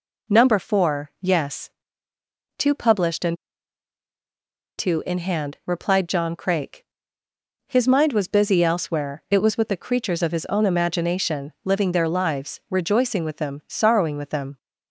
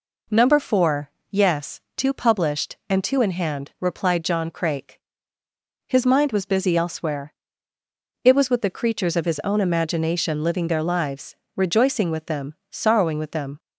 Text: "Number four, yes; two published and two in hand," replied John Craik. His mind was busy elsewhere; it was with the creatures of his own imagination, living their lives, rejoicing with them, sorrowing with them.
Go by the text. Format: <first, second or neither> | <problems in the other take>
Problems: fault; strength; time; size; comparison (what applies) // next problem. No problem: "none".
second | pauses between "and" and "two"; strong; at 3.3 s; 1.4 s long